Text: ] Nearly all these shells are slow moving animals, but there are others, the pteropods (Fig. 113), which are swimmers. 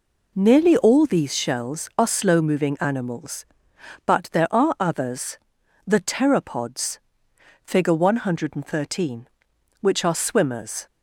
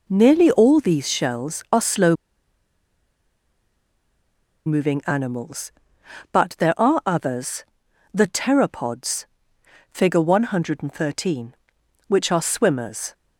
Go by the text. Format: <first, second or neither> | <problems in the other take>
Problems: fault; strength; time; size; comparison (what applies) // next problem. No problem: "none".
first | pauses between "slow" and "moving"; strong; at 2.1 s; 2.5 s long